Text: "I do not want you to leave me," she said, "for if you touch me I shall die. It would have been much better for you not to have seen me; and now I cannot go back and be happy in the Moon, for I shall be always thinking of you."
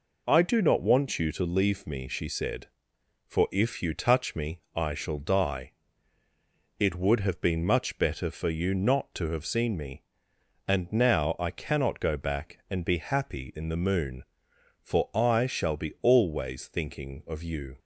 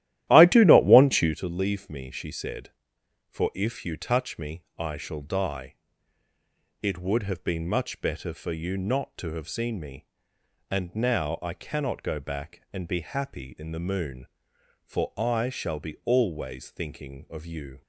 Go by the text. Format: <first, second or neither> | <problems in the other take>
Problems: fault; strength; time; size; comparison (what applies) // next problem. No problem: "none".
first | starts louder than the rest; strong; until 1.3 s; 13.5 dB